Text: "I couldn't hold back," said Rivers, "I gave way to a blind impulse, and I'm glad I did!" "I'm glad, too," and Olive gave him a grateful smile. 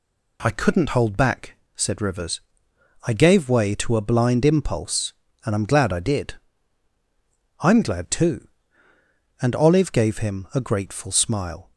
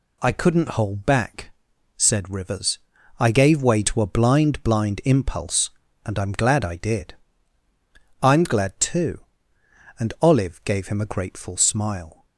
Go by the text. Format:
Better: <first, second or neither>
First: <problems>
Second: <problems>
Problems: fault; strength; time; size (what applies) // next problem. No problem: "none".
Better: first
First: none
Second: says "blind" twice; at 4.6 s